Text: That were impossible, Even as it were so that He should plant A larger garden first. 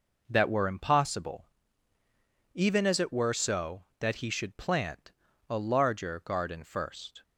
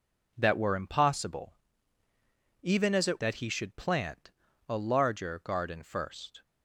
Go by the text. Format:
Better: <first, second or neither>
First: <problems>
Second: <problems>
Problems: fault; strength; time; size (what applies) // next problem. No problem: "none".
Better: first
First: pauses between "plant" and "A"; at 5.1 s; 0.38 s long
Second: skips "were so"; at 3.1 s // pauses between "plant" and "A"; at 4.3 s; 0.38 s long